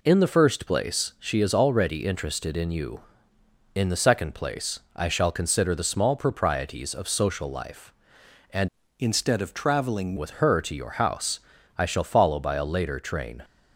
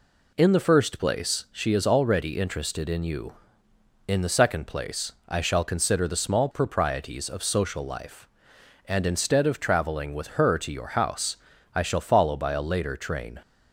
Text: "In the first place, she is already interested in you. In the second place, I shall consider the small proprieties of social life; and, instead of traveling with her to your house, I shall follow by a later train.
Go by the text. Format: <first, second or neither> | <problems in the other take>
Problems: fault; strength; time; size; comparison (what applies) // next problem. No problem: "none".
second | changes voice from "instead" to "traveling"; from 8.9 to 10.1 s; 1.2 s long